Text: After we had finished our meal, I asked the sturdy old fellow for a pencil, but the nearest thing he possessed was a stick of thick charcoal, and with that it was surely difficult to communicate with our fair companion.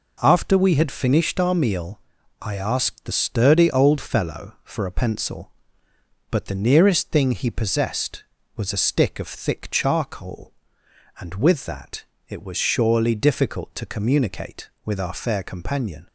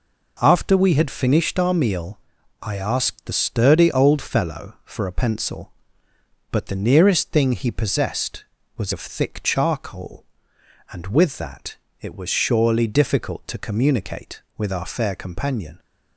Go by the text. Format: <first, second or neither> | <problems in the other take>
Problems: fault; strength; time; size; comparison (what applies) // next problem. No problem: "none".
first | skips "a stick"; at 8.9 s // pauses between "that" and "it"; slight; at 11.7 s; 0.26 s long; slight in the first